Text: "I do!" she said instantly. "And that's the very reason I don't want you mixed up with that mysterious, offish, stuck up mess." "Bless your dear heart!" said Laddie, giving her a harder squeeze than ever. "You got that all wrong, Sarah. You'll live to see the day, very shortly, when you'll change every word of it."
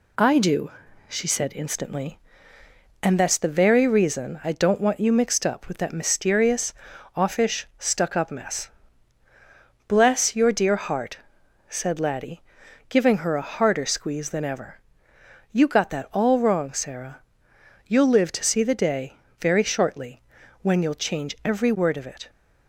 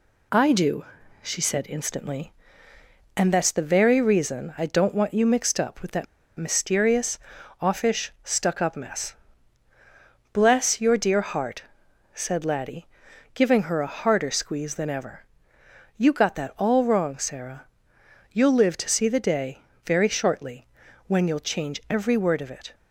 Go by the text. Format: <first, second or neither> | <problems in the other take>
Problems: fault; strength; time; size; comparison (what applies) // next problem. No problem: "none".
first | pauses between "that" and "mysterious"; slight; at 6.0 s; 0.32 s long